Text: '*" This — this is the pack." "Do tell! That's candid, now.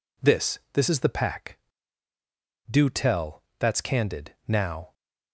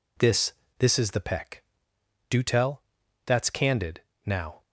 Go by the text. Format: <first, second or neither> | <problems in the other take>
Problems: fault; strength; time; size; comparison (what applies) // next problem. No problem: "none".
first | says "peck" for "pack"; at 1.2 s